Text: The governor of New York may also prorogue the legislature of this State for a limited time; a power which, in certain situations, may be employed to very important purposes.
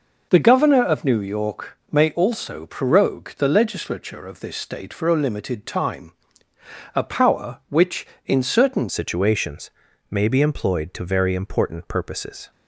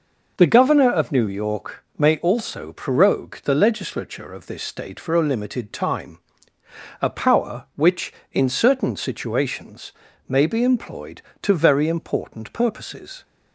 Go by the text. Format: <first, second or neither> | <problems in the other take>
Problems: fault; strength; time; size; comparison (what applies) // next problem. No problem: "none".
second | changes voice at "situations"; from 8.8 s on; 3.7 s long